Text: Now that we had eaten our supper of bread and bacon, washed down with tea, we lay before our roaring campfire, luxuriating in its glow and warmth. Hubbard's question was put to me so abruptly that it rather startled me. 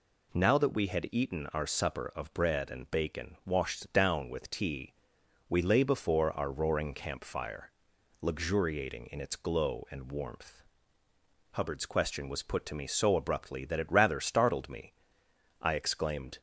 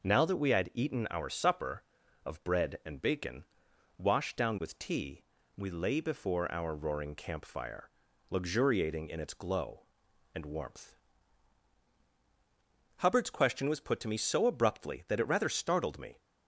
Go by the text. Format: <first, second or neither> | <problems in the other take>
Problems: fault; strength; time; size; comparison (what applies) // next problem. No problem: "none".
second | goes on to say "I exclaimed"; noticeable; from 15.6 s on; 0.78 s long